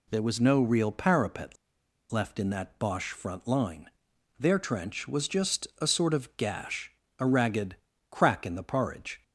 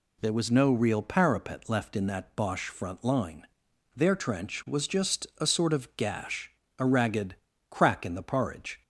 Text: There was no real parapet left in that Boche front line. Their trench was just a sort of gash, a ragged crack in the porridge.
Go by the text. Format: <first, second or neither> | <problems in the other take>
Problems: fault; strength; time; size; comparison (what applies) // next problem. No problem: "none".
second | pauses between "parapet" and "left"; noticeable; at 1.5 s; 0.56 s long // pauses between "ragged" and "crack"; slight; at 7.7 s; 0.34 s long; slight in the second